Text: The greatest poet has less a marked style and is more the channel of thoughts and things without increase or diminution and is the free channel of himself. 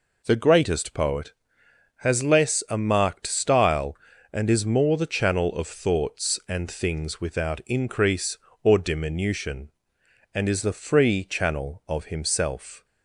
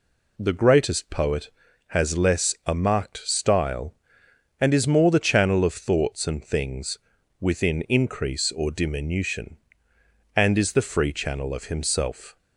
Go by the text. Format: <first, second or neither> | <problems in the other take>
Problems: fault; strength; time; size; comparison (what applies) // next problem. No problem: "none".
first | says "within" for "without"; at 7.3 s